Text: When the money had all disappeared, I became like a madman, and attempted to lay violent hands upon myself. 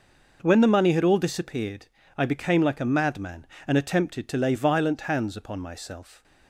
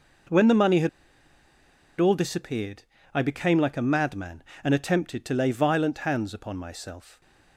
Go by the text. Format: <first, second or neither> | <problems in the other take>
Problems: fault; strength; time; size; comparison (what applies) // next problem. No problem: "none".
first | pauses between "had" and "all"; at 0.8 s; 1.1 s long